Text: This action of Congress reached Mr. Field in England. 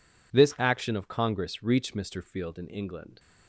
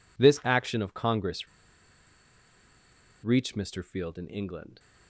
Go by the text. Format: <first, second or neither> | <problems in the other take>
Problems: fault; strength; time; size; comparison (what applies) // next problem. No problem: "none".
first | pauses between "Congress" and "reached"; strong; at 1.4 s; 1.7 s long